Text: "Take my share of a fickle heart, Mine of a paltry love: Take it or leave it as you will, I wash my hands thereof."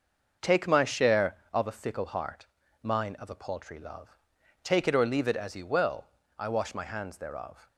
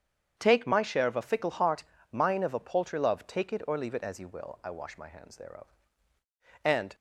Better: first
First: starts louder than the rest; noticeable; until 1.5 s; 6 dB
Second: starts louder than the rest; strong; until 1.3 s; 8 dB // goes on to say "And"; slight; from 6.6 s on; 0.32 s long

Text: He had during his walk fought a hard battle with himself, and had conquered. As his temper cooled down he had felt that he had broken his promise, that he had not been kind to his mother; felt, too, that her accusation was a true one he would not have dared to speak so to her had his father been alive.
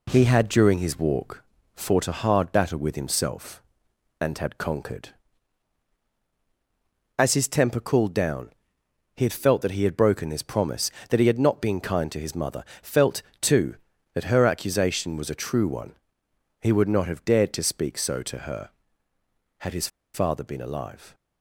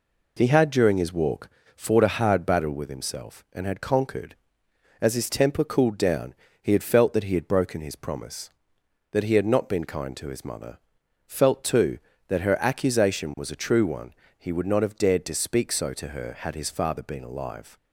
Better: second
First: pauses between "walk" and "fought"; slight; at 1.4 s; 0.32 s long // pauses between "down" and "he"; noticeable; at 8.4 s; 0.68 s long // pauses between "one" and "he"; noticeable; at 15.9 s; 0.70 s long // pauses between "his" and "father"; slight; at 19.8 s; 0.25 s long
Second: pauses between "walk" and "fought"; slight; at 1.4 s; 0.26 s long // pauses between "down" and "he"; slight; at 6.3 s; 0.26 s long // pauses between "one" and "he"; slight; at 14.1 s; 0.24 s long

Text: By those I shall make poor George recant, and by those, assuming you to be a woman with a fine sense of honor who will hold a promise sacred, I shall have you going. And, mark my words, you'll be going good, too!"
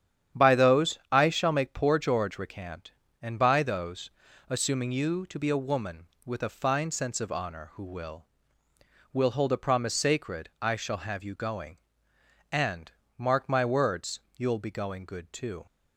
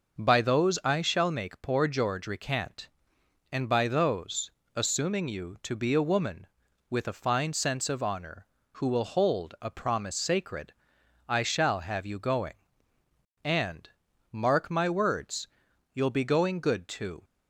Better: second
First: starts louder than the rest; strong; until 1.5 s; 9.5 dB // says "will" twice; at 9.1 s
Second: none

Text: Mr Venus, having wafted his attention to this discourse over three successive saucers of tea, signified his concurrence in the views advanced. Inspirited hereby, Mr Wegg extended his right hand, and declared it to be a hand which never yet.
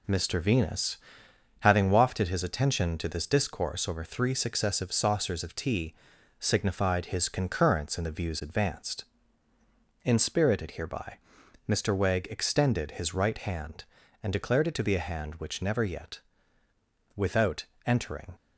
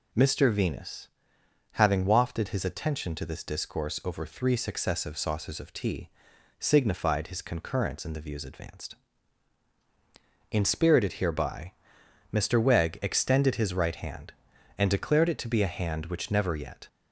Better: second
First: goes on to say "Without entering"; noticeable; from 17.1 s on; 1.2 s long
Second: none

